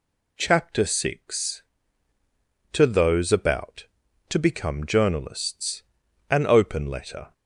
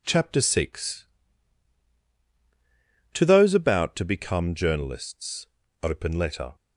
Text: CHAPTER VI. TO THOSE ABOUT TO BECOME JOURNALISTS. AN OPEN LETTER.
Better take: first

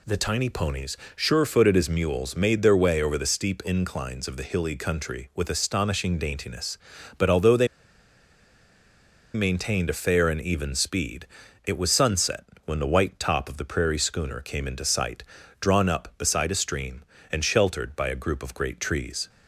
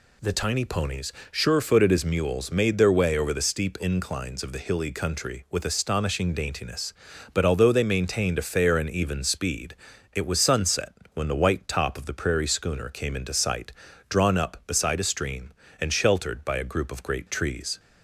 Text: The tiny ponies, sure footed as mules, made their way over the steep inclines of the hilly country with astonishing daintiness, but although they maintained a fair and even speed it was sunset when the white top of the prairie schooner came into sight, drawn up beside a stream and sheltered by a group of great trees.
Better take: second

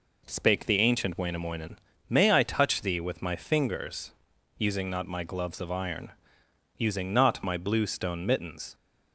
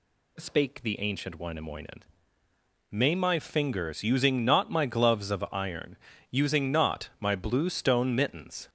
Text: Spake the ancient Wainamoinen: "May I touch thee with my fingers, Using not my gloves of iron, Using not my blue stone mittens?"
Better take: first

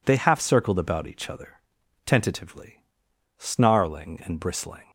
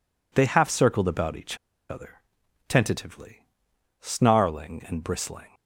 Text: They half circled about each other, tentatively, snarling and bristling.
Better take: first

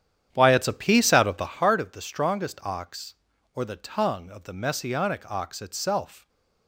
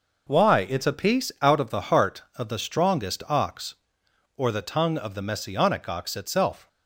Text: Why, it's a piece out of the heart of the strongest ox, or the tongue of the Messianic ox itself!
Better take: second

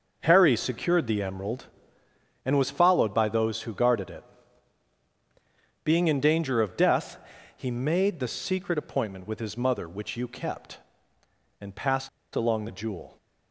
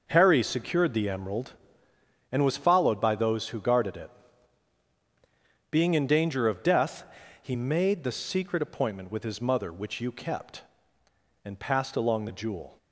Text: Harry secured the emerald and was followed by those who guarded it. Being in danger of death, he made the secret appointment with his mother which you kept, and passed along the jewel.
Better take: second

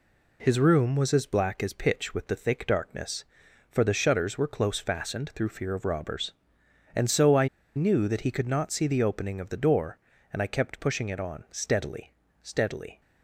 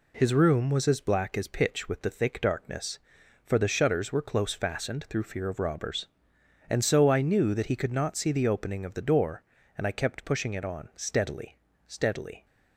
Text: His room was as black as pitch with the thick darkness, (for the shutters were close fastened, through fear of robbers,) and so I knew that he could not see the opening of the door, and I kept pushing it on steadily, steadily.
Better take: second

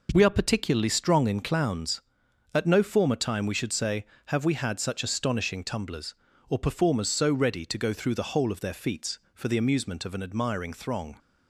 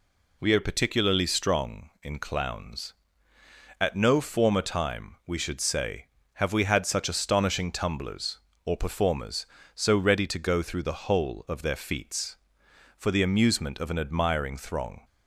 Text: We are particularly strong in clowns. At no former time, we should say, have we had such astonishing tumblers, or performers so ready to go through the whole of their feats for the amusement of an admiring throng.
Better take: neither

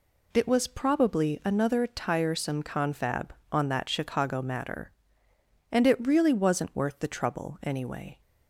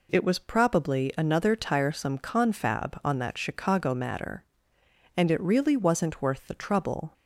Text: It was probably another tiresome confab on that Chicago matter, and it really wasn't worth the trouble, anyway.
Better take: first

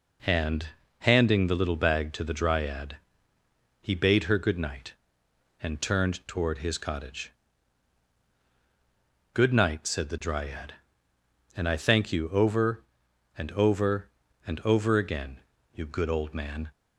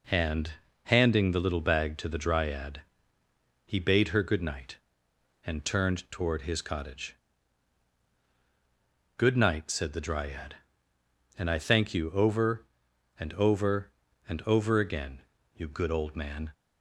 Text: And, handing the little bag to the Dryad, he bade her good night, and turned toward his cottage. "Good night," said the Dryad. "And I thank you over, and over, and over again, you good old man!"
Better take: neither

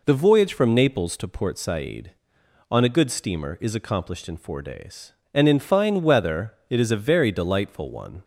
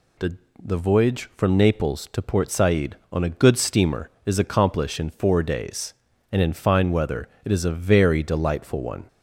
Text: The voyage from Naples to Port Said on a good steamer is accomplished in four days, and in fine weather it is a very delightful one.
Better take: first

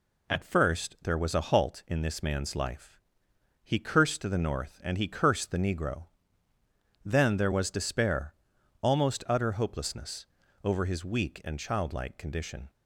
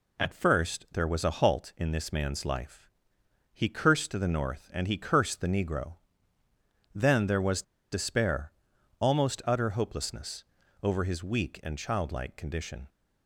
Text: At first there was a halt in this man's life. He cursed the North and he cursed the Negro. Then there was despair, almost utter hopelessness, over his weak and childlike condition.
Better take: first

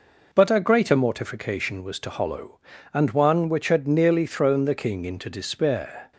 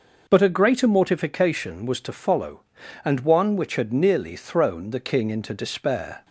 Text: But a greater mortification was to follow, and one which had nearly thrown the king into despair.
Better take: second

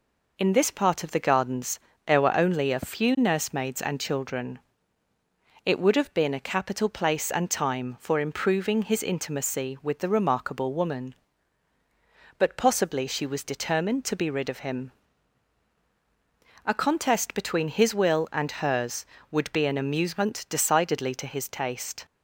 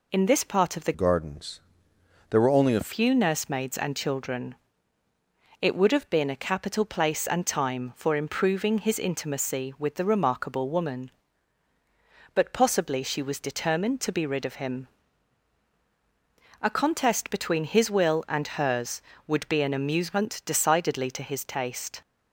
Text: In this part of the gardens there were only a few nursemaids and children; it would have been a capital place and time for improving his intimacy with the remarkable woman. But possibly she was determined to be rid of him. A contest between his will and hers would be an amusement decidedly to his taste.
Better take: first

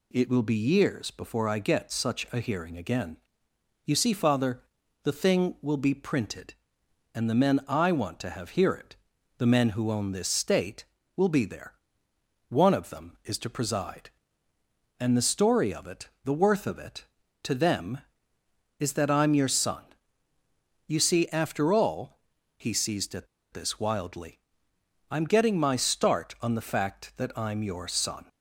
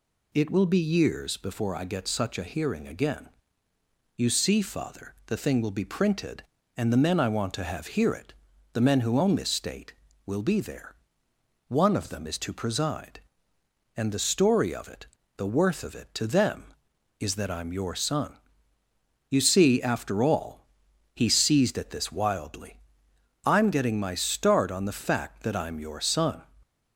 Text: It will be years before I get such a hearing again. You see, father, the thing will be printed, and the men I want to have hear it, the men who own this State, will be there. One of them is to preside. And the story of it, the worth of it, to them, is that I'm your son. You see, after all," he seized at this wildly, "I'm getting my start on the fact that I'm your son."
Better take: second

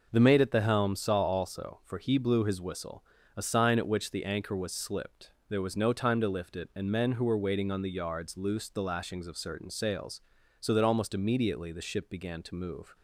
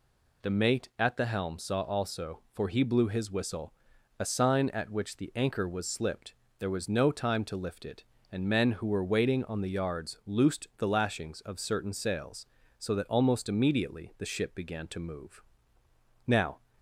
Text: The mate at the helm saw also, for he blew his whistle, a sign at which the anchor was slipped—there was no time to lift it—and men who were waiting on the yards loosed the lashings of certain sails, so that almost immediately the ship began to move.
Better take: first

